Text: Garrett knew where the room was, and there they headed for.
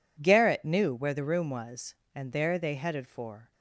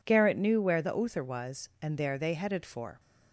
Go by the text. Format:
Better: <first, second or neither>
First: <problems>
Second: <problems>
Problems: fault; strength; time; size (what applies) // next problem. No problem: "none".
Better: first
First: none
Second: says "uther" for "room"; at 0.9 s